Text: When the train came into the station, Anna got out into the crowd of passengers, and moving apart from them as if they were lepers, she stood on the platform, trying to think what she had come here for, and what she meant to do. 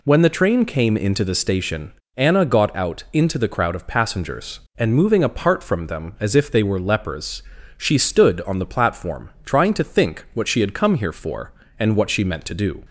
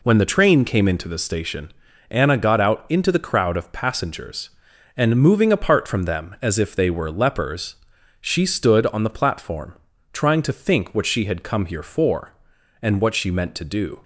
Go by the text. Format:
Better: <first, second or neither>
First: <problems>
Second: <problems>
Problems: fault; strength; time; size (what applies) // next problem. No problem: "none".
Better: neither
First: none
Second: none